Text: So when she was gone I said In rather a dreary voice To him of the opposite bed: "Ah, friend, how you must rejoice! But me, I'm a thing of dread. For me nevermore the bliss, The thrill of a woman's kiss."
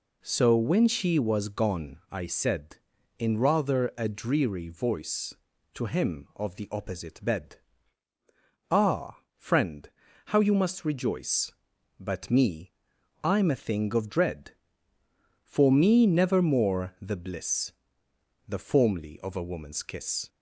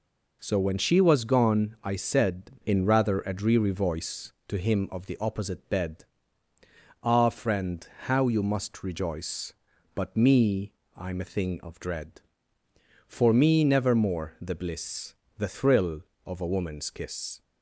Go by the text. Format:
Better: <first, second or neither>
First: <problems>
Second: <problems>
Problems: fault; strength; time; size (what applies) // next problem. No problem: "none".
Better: second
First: says "formly" for "thrill"; at 18.5 s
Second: none